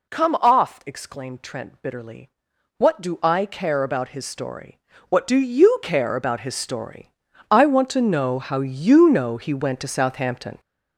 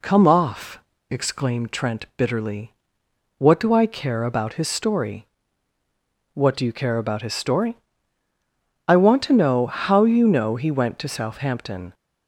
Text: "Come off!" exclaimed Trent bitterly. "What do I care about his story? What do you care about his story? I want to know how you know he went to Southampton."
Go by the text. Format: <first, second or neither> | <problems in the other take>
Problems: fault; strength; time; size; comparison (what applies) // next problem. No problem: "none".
second | gets louder; throughout; 6.5 dB